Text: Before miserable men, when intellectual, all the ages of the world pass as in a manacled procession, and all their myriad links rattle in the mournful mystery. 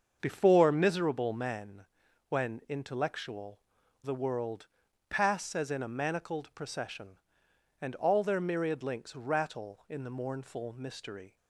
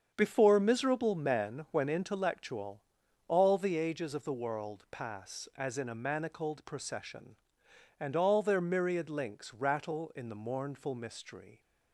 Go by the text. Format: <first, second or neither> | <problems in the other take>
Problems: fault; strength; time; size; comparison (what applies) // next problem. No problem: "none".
second | starts louder than the rest; until 1.2 s; 6.5 dB; strong in the second // skips "all the ages of"; at 3.8 s // pauses between "world" and "pass"; at 4.6 s; 0.44 s long